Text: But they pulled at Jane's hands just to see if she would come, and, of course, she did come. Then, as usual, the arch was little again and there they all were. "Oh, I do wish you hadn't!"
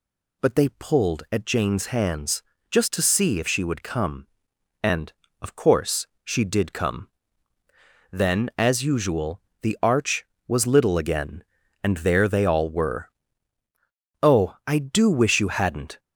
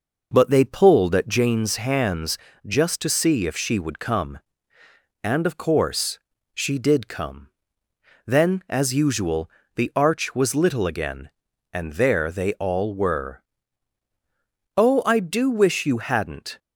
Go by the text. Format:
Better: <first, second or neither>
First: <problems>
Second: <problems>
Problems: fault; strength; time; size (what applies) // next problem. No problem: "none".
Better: first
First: pauses between "hands" and "just"; slight; at 2.4 s; 0.28 s long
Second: starts louder than the rest; noticeable; until 1.4 s; 5.5 dB // pauses between "hands" and "just"; slight; at 2.3 s; 0.28 s long